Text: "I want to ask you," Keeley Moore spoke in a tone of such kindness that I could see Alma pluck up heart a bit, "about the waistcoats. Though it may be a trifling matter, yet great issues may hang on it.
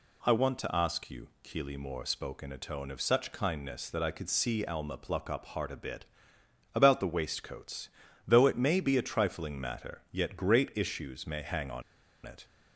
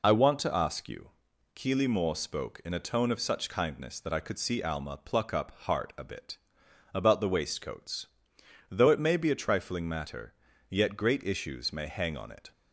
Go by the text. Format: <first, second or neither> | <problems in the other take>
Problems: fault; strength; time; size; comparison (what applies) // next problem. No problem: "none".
second | pauses between "on" and "it"; at 11.8 s; 0.44 s long